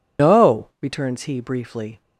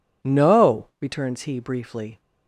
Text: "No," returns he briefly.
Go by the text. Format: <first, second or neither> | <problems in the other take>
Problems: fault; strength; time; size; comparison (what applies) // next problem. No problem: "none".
second | loses the start of "No"; at 0.1 s; 150 ms